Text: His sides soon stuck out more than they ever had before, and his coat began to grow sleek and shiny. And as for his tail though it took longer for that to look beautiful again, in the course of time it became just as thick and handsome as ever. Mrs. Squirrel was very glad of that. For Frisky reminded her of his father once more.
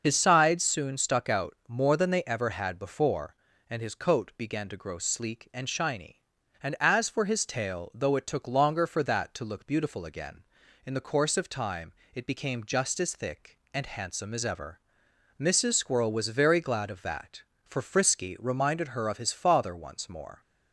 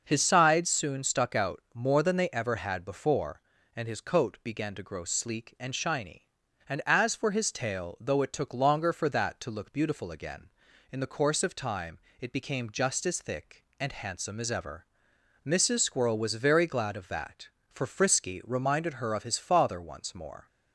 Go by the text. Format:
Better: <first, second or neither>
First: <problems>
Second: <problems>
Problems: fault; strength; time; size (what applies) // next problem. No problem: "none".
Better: second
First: loses the start of "His"; at 0.0 s; 55 ms // starts louder than the rest; until 1.0 s; 6 dB // pauses between "time" and "it"; slight; at 11.9 s; 0.24 s long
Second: starts louder than the rest; noticeable; until 1.0 s; 6 dB // pauses between "time" and "it"; slight; at 11.9 s; 0.24 s long